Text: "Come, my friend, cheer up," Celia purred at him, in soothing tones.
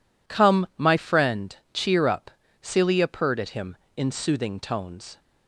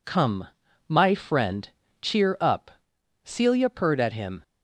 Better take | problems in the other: first | stops before "in soothing tones"; at 4.4 s

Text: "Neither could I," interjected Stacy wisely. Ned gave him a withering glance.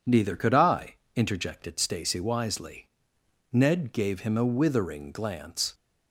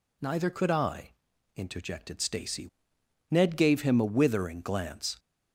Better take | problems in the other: first | skips "wisely"; at 2.9 s

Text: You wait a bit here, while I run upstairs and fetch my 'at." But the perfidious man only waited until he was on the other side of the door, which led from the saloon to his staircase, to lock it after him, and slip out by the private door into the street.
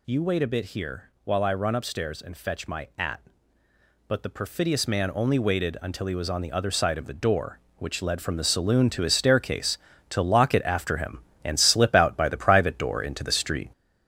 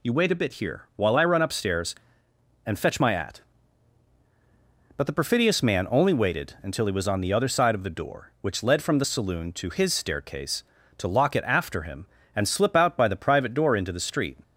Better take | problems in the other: second | gets louder; noticeable; throughout; 4.5 dB

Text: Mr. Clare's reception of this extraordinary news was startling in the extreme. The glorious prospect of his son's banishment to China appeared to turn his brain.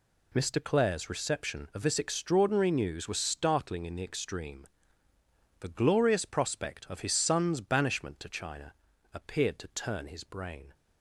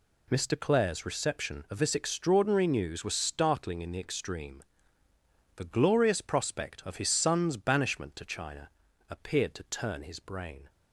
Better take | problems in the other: neither | pauses between "China" and "appeared"; the same in both

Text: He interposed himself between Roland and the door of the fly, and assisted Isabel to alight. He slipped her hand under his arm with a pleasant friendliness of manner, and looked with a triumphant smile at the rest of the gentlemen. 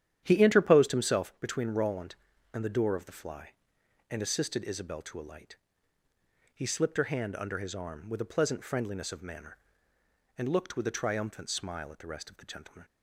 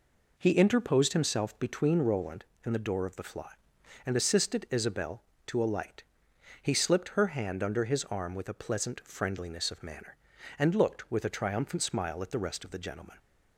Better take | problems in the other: second | starts louder than the rest; strong; until 1.3 s; 10.5 dB

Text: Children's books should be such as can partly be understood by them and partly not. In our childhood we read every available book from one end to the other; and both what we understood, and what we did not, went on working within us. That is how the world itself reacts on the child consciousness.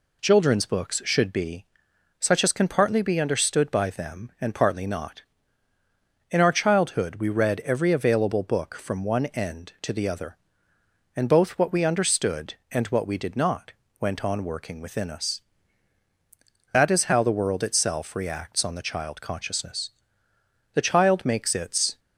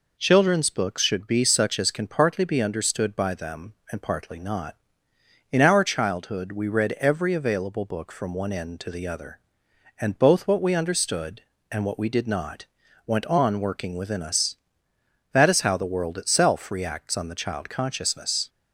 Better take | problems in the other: second | pauses between "be" and "such"; noticeable; at 1.6 s; 0.56 s long // goes on to say "The child makes its"; noticeable; from 20.7 s on; 1.2 s long

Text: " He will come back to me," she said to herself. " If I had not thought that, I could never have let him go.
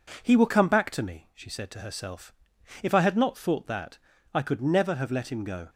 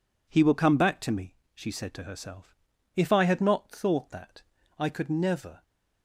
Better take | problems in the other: first | stops before "have let him go"; at 5.6 s

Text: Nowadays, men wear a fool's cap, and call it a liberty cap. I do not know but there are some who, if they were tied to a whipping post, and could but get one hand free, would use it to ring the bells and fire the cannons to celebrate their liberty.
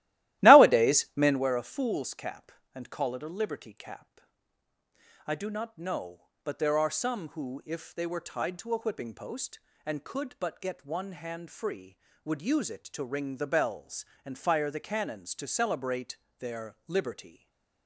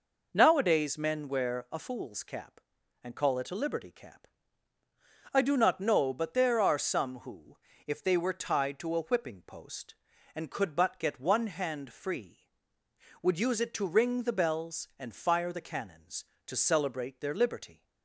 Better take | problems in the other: second | starts louder than the rest; strong; until 1.4 s; 15.5 dB // pauses between "celebrate" and "their"; slight; at 16.1 s; 0.24 s long // stays silent after the last word; slight; from 17.2 s on; 0.6 s long

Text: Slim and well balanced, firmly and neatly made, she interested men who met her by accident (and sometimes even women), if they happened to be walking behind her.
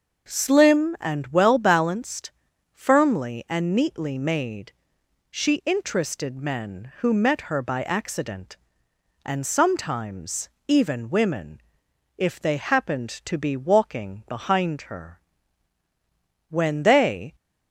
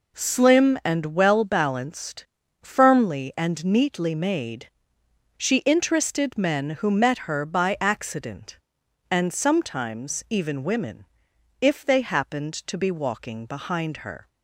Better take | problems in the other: second | pauses between "sometimes" and "even"; slight; at 10.4 s; 0.18 s long // goes on to say "When they"; noticeable; from 16.4 s on; 0.86 s long

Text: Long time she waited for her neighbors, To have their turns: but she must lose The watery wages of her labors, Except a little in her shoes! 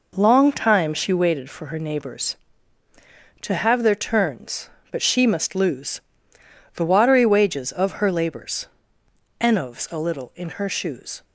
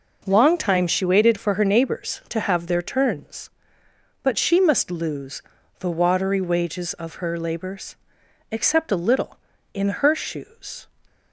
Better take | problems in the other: second | pauses between "lose" and "The"; noticeable; at 6.0 s; 0.74 s long; also in the second // says "Enovs" for "Except"; at 9.3 s

